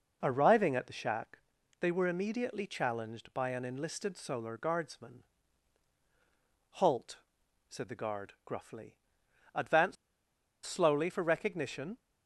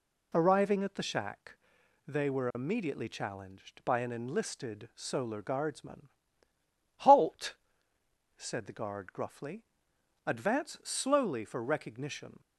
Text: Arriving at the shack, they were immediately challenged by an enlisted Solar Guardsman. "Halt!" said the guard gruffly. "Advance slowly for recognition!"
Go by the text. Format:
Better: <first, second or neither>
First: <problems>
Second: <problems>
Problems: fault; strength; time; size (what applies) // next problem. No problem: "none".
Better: second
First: pauses between "Advance" and "slowly"; noticeable; at 9.9 s; 0.70 s long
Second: none